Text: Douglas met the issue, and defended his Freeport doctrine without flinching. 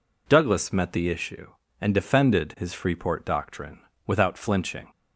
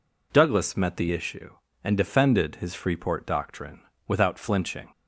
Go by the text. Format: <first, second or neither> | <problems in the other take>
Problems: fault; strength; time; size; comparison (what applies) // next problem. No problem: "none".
neither | pauses between "doctrine" and "without"; slight; the same in both